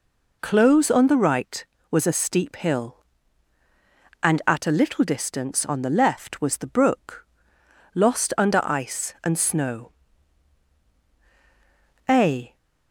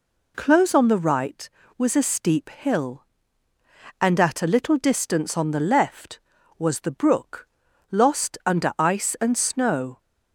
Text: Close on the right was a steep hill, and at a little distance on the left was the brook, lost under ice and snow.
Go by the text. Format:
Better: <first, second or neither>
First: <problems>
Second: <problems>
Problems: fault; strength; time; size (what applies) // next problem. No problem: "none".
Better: second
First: goes on to say "A"; slight; from 12.0 s on; 0.48 s long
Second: none